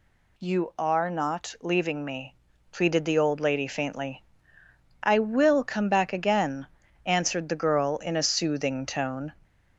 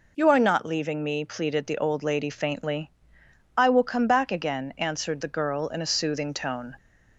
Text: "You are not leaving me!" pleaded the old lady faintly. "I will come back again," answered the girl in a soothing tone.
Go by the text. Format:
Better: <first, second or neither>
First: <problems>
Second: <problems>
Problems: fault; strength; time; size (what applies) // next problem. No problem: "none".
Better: neither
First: none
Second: none